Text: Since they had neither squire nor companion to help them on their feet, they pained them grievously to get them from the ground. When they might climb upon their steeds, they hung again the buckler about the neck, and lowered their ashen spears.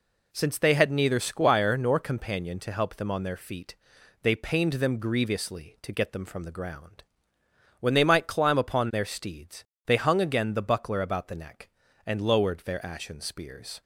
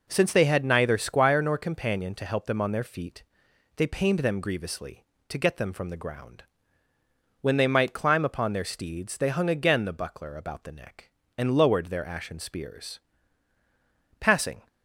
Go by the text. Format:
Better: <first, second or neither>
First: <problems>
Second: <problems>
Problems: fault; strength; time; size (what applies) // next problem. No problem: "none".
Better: first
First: none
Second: goes on to say "Passing"; slight; from 14.1 s on; 0.48 s long